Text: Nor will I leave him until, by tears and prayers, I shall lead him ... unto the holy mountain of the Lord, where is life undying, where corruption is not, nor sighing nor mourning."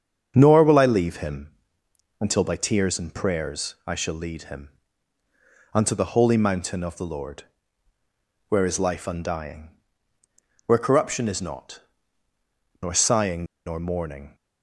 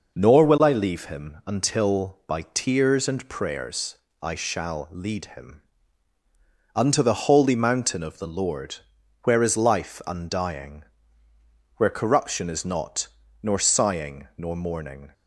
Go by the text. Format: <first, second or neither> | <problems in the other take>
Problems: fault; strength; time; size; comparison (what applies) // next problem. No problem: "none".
second | starts louder than the rest; until 1.3 s; 7 dB // pauses between "him" and "until"; noticeable; at 1.4 s; 0.72 s long // pauses between "sighing" and "nor"; slight; at 13.4 s; 0.21 s long